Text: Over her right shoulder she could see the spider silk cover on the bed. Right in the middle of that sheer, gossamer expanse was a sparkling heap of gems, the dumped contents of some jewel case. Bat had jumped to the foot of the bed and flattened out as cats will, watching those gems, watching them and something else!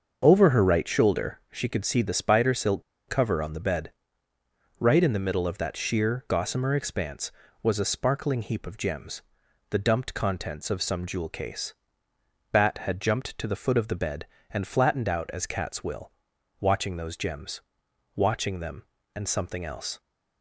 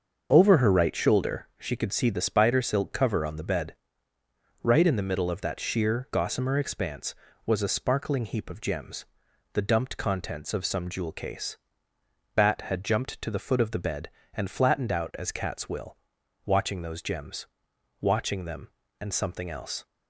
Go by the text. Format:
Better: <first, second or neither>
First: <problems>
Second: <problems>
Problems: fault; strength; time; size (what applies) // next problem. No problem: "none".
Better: second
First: starts louder than the rest; until 1.2 s; 6.5 dB // pauses between "silk" and "cover"; slight; at 2.8 s; 0.26 s long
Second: starts louder than the rest; until 1.3 s; 6.5 dB